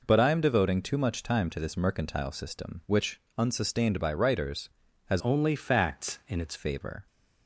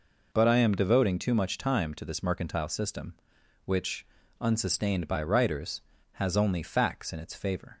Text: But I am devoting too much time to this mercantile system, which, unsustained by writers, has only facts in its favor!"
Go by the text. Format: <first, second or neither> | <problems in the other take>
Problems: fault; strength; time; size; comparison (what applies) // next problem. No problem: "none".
second | changes voice from "only" to "its"; from 5.1 to 6.5 s; 1.4 s long